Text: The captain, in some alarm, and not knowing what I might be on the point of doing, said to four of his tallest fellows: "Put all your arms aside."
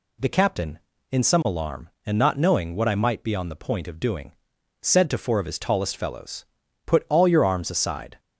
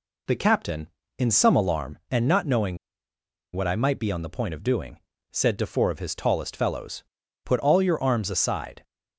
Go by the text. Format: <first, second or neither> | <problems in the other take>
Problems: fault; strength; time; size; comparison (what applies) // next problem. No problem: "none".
first | pauses between "knowing" and "what"; noticeable; at 2.7 s; 0.78 s long